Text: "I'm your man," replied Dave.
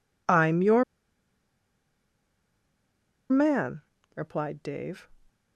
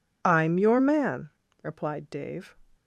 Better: second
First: pauses between "your" and "man"; strong; at 0.8 s; 2.4 s long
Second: none

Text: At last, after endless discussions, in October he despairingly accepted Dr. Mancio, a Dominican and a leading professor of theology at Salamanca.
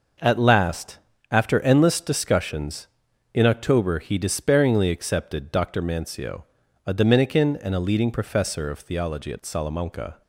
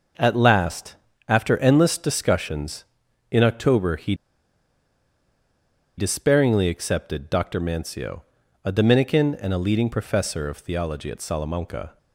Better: first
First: none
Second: pauses between "he" and "despairingly"; strong; at 4.1 s; 1.8 s long

